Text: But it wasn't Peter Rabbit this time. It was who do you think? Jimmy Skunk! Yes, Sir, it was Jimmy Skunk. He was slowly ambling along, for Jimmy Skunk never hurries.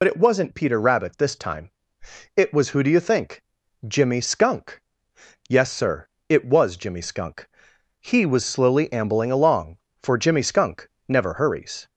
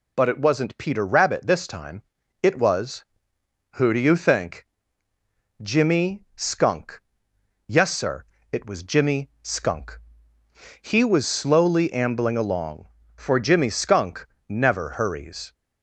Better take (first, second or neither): second